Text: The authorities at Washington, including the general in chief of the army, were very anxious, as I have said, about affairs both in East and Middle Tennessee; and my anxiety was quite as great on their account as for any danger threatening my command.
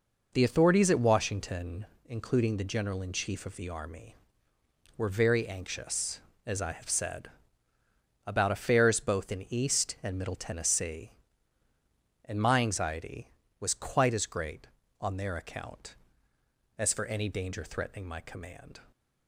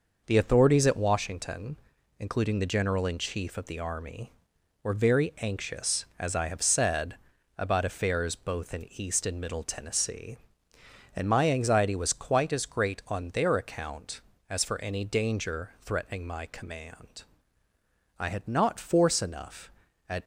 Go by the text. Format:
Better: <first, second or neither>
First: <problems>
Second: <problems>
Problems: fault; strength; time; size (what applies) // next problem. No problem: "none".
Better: first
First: none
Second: goes on to say "I had not force enough at"; strong; from 18.1 s on; 2.0 s long